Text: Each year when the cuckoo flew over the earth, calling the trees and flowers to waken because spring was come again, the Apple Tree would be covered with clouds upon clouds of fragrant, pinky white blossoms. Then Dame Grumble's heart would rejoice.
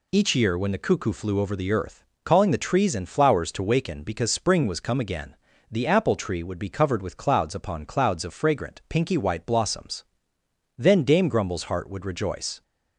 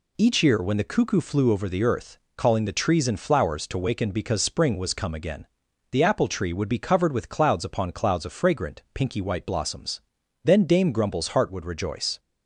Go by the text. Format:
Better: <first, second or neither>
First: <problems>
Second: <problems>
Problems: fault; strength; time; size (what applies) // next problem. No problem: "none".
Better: neither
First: none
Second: none